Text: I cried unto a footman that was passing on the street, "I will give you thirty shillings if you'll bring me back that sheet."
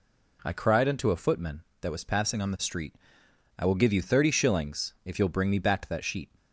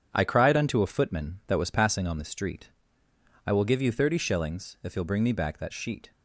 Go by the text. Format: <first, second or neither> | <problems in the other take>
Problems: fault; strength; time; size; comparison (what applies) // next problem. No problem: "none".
neither | none